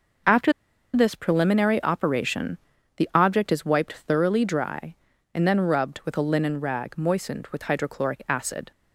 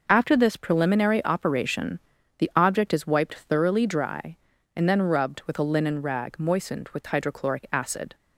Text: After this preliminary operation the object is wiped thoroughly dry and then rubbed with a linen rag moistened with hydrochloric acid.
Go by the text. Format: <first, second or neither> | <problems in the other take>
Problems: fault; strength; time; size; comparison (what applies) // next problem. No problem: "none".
second | pauses between "After" and "this"; at 0.5 s; 0.42 s long // pauses between "operation" and "the"; at 2.5 s; 0.40 s long; also in the second